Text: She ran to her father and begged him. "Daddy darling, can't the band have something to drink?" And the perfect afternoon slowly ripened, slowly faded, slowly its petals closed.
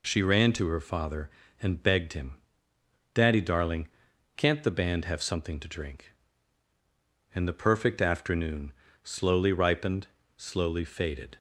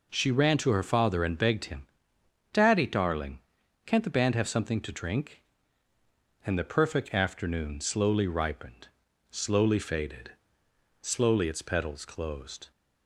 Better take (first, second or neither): second